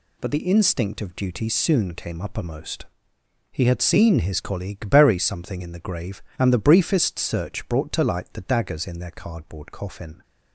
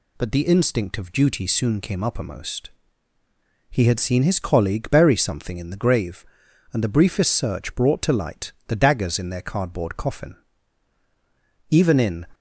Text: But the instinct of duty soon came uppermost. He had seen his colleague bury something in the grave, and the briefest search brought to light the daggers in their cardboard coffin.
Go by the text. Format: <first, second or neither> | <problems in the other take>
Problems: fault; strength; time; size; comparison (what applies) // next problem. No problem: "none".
first | pauses between "light" and "the"; slight; at 8.5 s; 0.16 s long // goes on to say "Even in"; from 11.6 s on; 0.56 s long